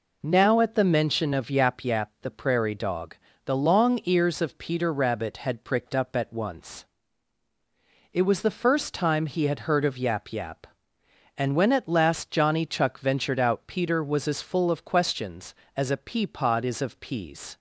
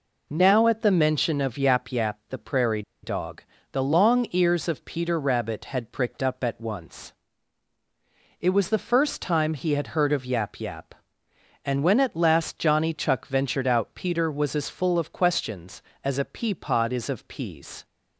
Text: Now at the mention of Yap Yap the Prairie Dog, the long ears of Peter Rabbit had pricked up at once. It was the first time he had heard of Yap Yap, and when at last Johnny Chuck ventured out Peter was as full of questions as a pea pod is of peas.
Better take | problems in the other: first | pauses between "Prairie" and "Dog"; slight; at 2.8 s; 0.21 s long

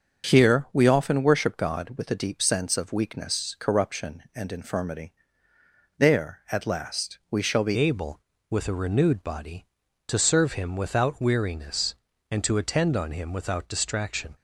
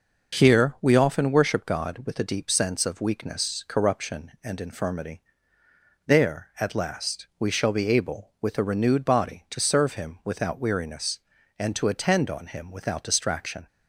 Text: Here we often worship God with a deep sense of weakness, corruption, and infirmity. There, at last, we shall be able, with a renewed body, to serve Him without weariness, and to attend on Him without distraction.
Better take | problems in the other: second | starts louder than the rest; until 1.3 s; 6.5 dB // changes voice at "able"; from 7.7 s on; 6.6 s long

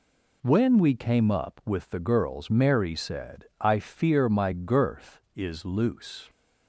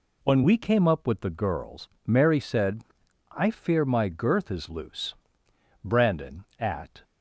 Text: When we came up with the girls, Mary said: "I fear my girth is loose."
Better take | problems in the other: first | goes on to say "Brandon at"; noticeable; from 5.8 s on; 1.2 s long

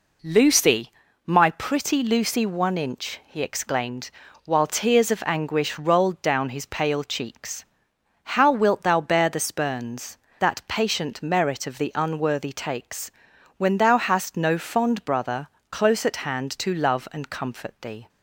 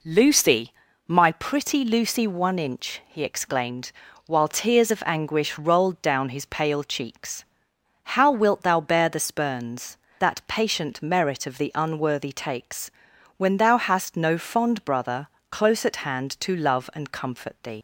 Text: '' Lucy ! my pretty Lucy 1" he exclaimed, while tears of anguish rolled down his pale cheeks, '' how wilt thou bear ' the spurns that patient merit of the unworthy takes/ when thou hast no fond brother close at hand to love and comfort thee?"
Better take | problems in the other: first | pauses between "brother" and "close"; slight; at 15.2 s; 0.22 s long; slight in the first // leaves "thee" unfinished; at 17.7 s; 90 ms

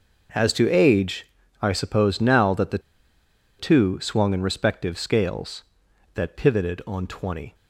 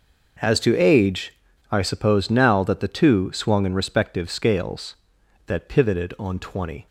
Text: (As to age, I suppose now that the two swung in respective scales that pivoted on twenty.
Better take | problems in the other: second | pauses between "the" and "two"; noticeable; at 2.7 s; 0.80 s long

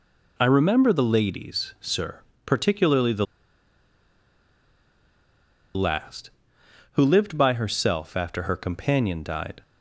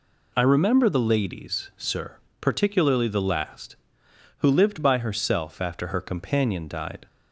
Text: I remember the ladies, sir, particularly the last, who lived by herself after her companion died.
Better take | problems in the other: second | pauses between "the" and "last"; strong; at 3.2 s; 2.5 s long

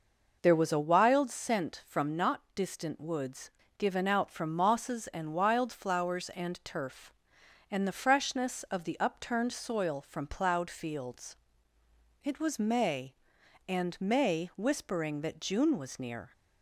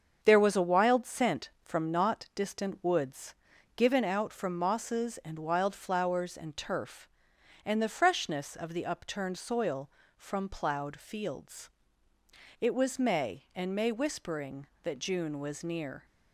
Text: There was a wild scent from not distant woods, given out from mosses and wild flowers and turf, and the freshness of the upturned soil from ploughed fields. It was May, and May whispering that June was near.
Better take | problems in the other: first | gets quieter; throughout; 6.5 dB

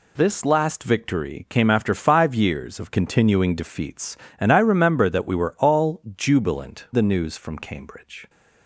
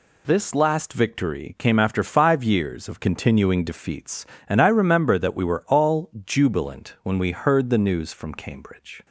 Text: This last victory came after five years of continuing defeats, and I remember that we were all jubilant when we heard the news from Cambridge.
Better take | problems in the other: second | pauses between "all" and "jubilant"; slight; at 6.0 s; 0.16 s long; slight in the second // skips "when we heard"; at 6.8 s

